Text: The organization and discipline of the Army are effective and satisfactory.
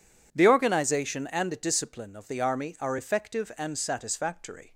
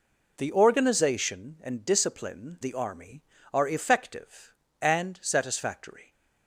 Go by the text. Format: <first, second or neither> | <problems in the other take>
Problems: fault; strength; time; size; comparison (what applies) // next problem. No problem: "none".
first | skips "of"; at 2.6 s